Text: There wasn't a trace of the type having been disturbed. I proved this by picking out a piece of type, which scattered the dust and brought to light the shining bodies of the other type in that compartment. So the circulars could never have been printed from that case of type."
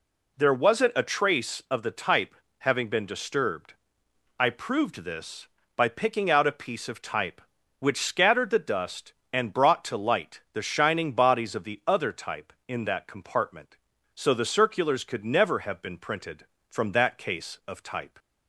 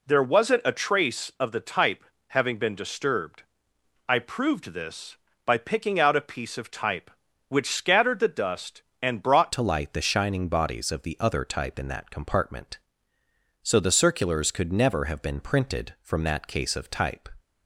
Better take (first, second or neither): first